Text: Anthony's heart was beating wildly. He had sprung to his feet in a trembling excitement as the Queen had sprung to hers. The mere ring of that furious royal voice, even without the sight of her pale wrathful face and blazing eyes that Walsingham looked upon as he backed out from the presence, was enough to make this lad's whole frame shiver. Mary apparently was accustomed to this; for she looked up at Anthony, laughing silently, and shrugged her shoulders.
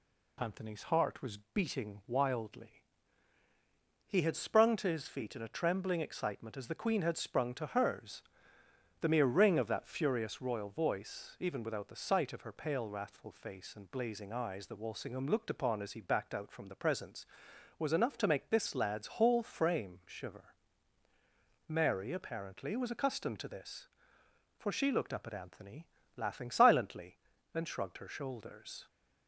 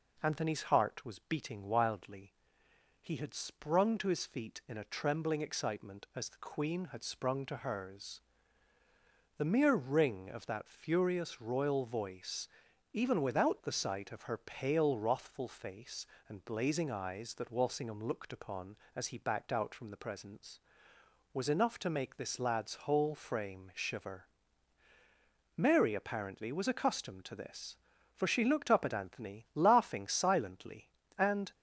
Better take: first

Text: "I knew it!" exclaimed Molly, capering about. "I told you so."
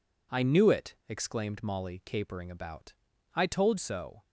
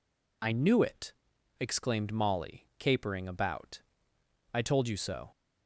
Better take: second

